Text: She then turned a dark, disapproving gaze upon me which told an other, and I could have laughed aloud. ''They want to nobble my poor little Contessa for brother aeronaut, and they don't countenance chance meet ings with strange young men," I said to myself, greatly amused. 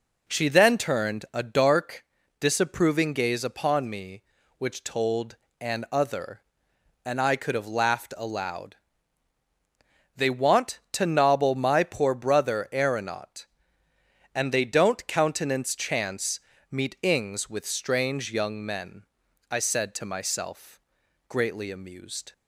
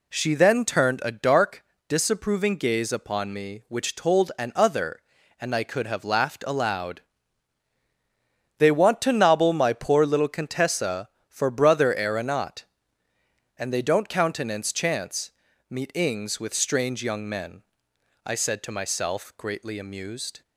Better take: second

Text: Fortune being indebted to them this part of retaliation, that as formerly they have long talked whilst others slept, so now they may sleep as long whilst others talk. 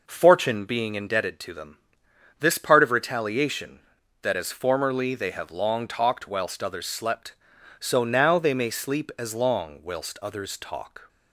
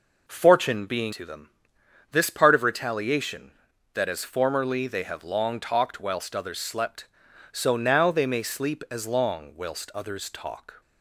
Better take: first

